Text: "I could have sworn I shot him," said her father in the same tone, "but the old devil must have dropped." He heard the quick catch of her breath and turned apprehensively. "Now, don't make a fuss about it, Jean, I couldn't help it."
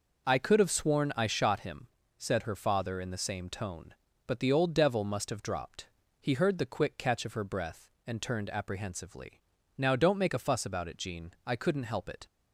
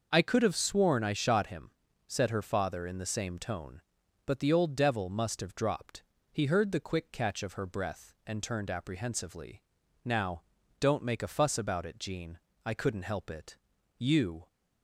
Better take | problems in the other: first | starts louder than the rest; noticeable; until 1.1 s; 6 dB // goes on to say "You"; from 13.9 s on; 0.50 s long

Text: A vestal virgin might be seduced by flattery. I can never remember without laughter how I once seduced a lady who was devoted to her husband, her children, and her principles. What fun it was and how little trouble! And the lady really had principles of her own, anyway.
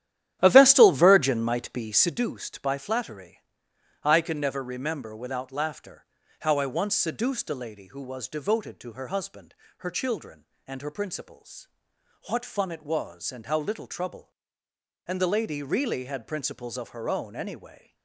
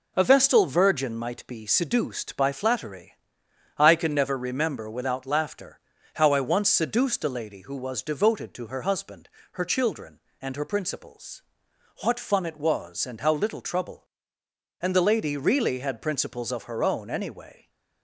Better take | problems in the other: second | starts louder than the rest; strong; until 2.2 s; 11.5 dB // pauses between "laughter" and "how"; slight; at 6.0 s; 0.34 s long; slight in the second

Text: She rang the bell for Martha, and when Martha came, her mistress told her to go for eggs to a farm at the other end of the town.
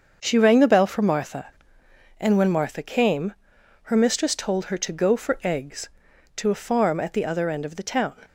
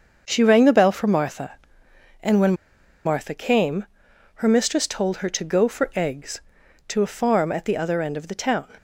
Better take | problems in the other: first | starts louder than the rest; until 1.2 s; 6.5 dB; also in the first // pauses between "when" and "Martha"; noticeable; at 2.5 s; 0.52 s long

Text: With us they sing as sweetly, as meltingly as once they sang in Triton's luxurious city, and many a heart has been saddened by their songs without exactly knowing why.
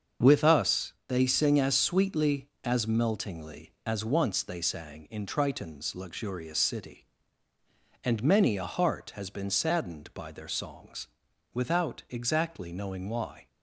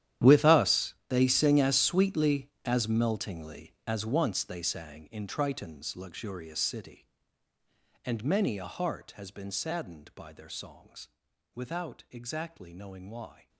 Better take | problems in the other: first | gets quieter; strong; throughout; 17.5 dB // starts louder than the rest; strong; until 1.3 s; 11 dB; also in the first // pauses between "songs" and "without"; noticeable; at 11.0 s; 0.48 s long; noticeable in the first

